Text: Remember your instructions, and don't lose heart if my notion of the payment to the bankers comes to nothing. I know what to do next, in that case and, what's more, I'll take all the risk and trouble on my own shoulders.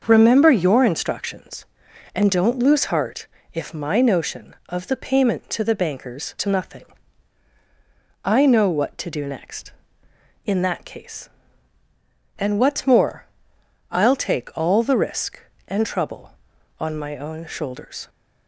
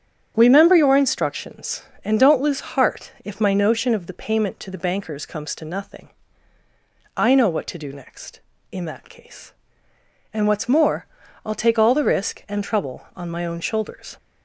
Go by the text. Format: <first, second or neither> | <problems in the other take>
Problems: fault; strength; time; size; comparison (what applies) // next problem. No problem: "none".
second | starts louder than the rest; until 1.0 s; 6.5 dB; strong in the second // pauses between "heart" and "if"; slight; at 3.2 s; 0.26 s long // skips "comes"; at 6.3 s